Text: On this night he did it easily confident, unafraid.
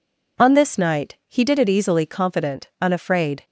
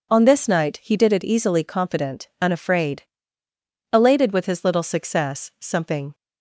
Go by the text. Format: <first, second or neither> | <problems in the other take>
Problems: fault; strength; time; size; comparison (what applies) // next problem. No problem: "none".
first | goes on to say "Elated with his little success something"; strong; from 3.9 s on; 2.2 s long